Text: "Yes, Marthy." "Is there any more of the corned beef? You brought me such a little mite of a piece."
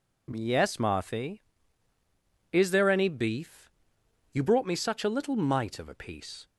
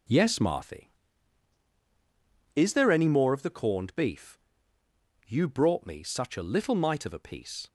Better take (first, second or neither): second